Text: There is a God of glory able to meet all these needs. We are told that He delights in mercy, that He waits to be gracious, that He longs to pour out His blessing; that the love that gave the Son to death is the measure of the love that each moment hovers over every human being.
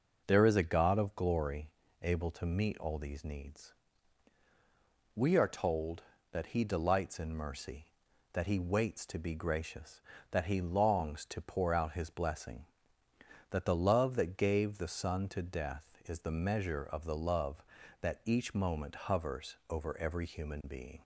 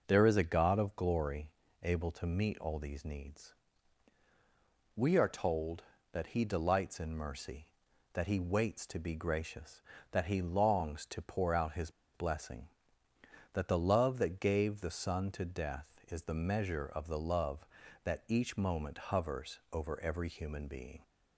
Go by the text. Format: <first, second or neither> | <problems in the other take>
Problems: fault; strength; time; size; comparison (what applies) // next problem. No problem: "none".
first | pauses between "glory" and "able"; slight; at 1.4 s; 0.34 s long; slight in the first // pauses between "His" and "blessing"; slight; at 11.9 s; 0.23 s long